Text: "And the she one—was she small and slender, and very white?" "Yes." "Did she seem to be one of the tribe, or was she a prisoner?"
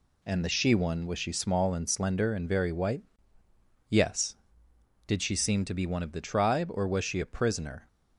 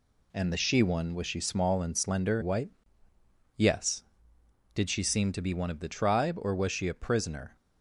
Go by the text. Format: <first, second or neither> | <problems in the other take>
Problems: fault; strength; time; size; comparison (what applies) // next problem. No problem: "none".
first | skips "and very"; at 2.4 s